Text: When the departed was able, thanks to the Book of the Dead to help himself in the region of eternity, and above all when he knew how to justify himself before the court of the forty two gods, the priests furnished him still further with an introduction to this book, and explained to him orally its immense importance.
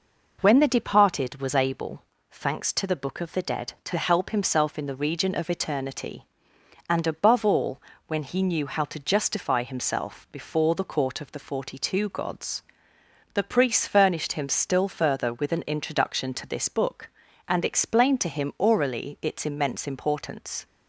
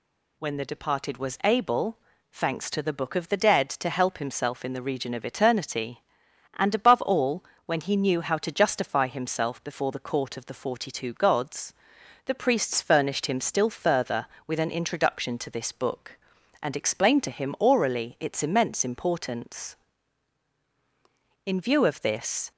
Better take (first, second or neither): first